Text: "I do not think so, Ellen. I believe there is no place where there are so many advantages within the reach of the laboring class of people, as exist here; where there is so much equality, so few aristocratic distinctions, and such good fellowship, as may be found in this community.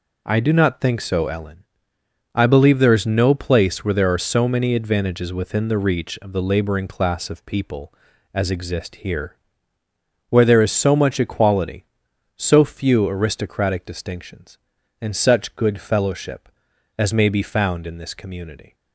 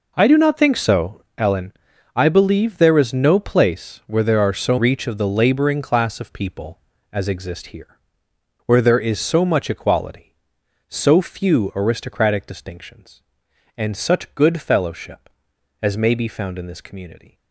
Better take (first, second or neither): first